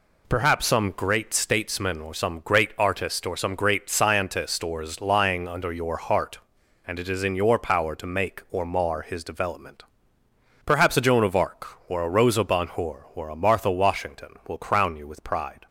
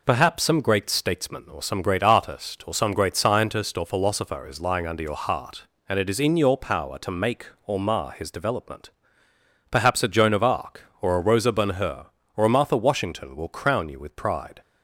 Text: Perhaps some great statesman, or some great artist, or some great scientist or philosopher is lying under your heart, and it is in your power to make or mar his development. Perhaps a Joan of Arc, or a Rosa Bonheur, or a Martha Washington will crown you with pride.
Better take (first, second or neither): second